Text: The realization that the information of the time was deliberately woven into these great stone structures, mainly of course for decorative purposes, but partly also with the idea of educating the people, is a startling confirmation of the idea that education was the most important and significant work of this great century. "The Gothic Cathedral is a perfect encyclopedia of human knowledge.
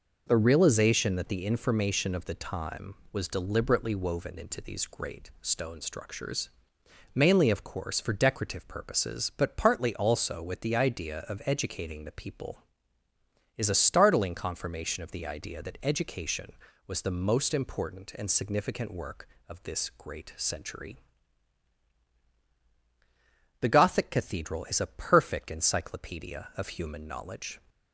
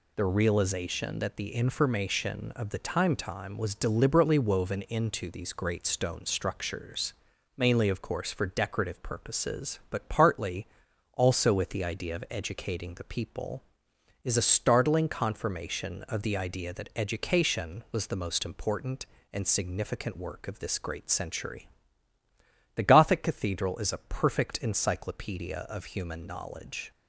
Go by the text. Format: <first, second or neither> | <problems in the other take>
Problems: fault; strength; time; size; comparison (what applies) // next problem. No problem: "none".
first | says "time" twice; at 3.1 s // pauses between "partly" and "also"; noticeable; at 10.6 s; 0.46 s long